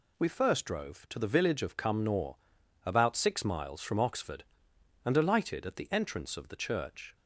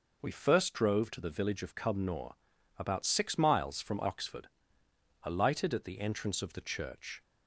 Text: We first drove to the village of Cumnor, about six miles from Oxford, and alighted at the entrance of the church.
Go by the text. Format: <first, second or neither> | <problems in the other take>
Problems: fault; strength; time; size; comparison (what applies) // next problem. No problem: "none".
first | skips "and"; at 4.8 s